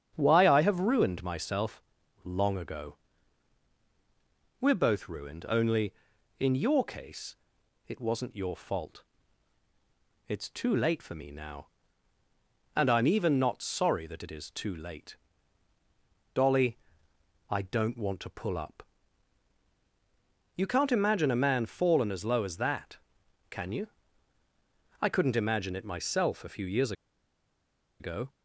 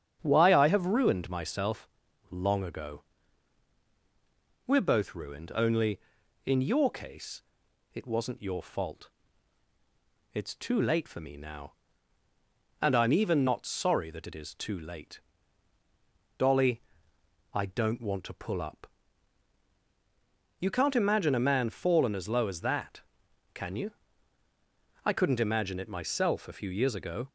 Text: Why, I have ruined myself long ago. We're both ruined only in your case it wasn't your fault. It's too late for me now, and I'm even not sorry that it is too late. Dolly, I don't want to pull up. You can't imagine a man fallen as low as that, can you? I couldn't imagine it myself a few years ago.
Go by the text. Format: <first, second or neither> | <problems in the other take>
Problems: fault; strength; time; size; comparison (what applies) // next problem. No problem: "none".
second | starts louder than the rest; strong; until 1.1 s; 8 dB; strong in the second // pauses between "myself" and "long"; at 1.8 s; 0.40 s long; also in the second // pauses between "case" and "it"; noticeable; at 7.3 s; 0.54 s long; noticeable in the second // pauses between "years" and "ago"; at 26.9 s; 1.0 s long